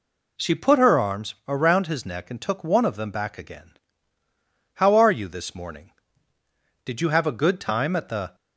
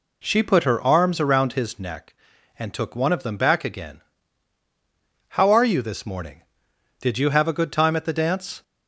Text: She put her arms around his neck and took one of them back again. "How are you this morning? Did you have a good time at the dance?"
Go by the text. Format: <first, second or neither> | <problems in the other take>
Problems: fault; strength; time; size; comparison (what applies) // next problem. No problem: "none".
second | stops before "dance"; at 8.3 s